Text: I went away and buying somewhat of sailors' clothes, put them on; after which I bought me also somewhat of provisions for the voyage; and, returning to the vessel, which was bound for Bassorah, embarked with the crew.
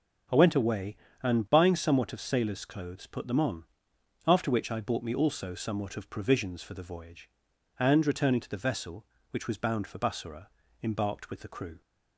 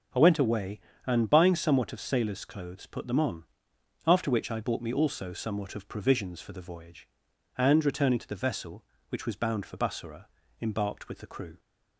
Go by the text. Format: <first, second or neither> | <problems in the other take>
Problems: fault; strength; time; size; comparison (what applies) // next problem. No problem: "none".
neither | starts louder than the rest; the same in both